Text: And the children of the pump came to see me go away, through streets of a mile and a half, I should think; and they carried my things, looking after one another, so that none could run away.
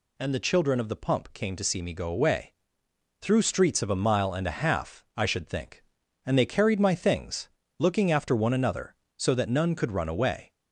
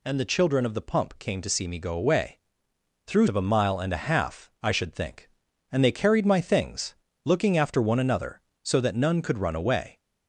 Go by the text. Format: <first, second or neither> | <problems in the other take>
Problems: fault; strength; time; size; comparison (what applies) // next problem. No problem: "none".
first | skips "streets"; at 3.2 s